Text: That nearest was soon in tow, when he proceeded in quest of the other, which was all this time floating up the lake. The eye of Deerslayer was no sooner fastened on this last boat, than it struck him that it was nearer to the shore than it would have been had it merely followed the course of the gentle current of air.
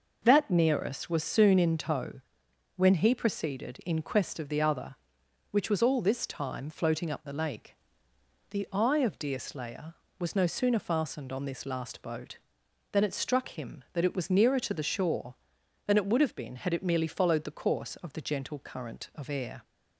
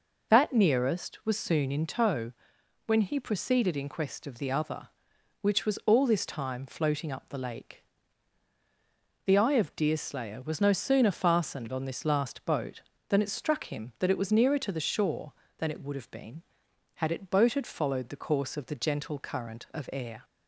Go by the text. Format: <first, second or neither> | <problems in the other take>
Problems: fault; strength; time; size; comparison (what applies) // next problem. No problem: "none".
first | says "boated" for "merely"; at 17.2 s